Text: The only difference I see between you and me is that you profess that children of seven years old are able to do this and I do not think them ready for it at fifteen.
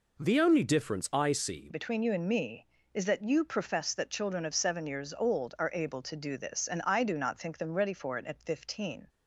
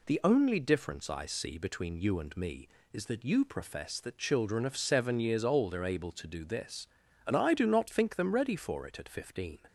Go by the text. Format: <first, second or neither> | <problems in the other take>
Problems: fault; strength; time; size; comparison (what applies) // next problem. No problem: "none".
second | changes voice at "between"; from 1.7 s on; 7.3 s long